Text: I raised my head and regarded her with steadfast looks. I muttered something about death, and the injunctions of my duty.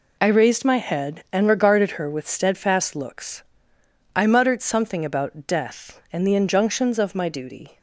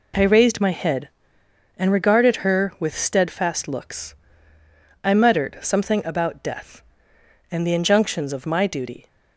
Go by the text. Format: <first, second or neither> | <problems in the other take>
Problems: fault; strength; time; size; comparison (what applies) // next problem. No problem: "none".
neither | none